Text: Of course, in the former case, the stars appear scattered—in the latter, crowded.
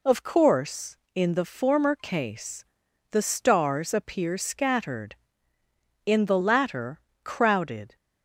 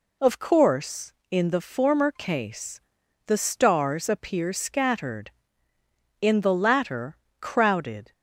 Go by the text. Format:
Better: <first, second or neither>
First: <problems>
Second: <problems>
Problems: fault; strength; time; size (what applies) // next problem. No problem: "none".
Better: neither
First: none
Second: none